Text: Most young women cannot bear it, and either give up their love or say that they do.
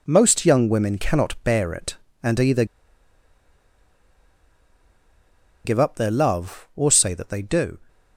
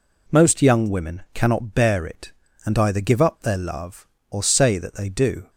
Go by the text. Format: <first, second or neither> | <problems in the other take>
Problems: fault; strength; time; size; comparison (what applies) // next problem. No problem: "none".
second | pauses between "either" and "give"; strong; at 2.6 s; 3.0 s long